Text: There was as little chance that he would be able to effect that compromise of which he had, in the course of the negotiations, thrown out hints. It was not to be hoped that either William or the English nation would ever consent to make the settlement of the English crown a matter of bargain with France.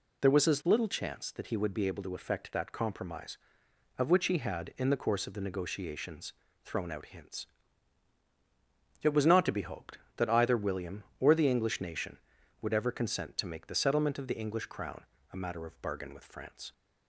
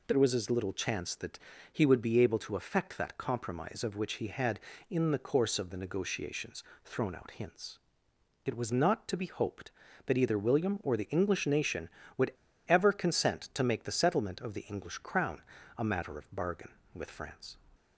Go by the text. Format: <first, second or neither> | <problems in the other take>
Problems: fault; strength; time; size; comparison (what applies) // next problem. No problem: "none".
first | pauses between "that" and "he"; slight; at 1.3 s; 0.34 s long // pauses between "would" and "ever"; slight; at 12.3 s; 0.34 s long // pauses between "crown" and "a"; slight; at 15.4 s; 0.36 s long; slight in the first